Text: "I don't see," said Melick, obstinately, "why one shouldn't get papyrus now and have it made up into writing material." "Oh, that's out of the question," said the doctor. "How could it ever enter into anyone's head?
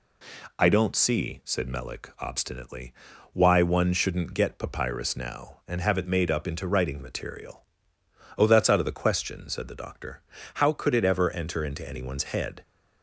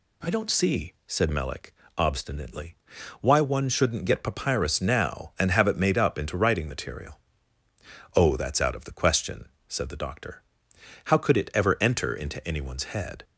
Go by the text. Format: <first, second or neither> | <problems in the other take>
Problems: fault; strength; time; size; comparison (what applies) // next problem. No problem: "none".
neither | none